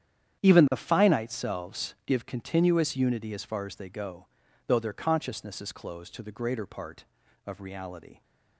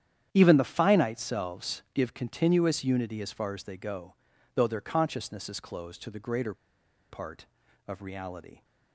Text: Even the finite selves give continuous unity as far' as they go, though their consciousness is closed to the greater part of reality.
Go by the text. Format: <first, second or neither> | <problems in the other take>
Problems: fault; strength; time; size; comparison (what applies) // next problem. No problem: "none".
first | starts louder than the rest; strong; until 1.3 s; 9.5 dB; strong in the first // pauses between "greater" and "part"; noticeable; at 6.5 s; 0.55 s long